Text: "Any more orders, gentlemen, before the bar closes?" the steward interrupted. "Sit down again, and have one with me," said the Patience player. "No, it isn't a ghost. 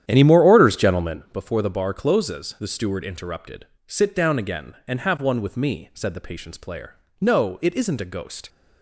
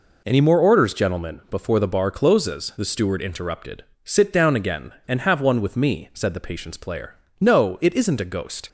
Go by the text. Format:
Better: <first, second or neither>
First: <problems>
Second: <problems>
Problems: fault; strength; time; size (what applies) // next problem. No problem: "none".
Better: second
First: starts louder than the rest; strong; until 1.3 s; 10 dB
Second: none